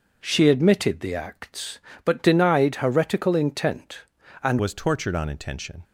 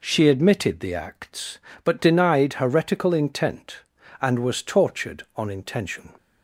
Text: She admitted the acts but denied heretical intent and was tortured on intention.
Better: second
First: changes voice at "was"; from 4.5 s on; 1.3 s long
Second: none

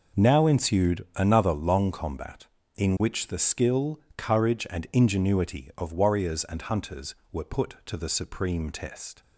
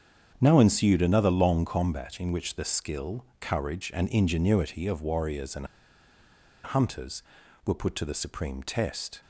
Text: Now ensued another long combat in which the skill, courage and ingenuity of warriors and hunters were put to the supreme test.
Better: first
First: none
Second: starts louder than the rest; strong; until 1.4 s; 7.5 dB // pauses between "and" and "hunters"; noticeable; at 5.6 s; 0.97 s long

